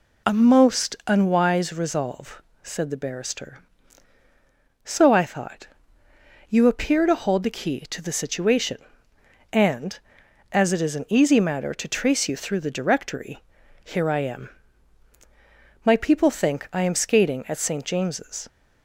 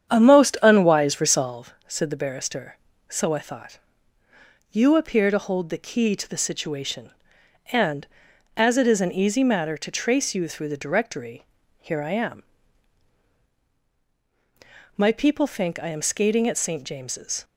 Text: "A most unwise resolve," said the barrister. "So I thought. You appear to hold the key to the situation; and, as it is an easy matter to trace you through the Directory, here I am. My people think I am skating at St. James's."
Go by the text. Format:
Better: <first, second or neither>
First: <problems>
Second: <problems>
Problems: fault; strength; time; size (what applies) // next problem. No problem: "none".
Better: first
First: none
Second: starts louder than the rest; strong; until 1.6 s; 8.5 dB